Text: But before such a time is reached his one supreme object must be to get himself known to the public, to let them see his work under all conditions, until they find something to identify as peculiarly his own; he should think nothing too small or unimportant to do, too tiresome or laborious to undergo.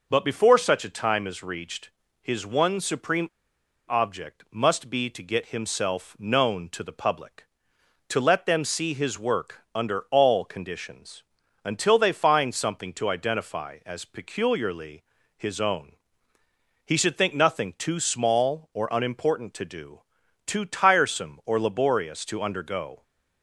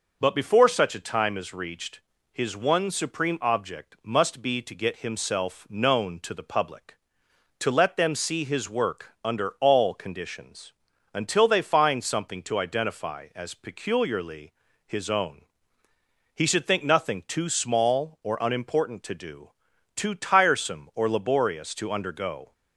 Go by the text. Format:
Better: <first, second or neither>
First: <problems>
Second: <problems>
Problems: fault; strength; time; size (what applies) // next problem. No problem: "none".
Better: second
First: pauses between "reached" and "his"; slight; at 1.9 s; 0.30 s long // pauses between "supreme" and "object"; noticeable; at 3.2 s; 0.62 s long // pauses between "work" and "under"; slight; at 9.5 s; 0.16 s long // pauses between "peculiarly" and "his"; slight; at 15.0 s; 0.34 s long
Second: pauses between "reached" and "his"; slight; at 2.0 s; 0.30 s long // pauses between "peculiarly" and "his"; slight; at 14.5 s; 0.34 s long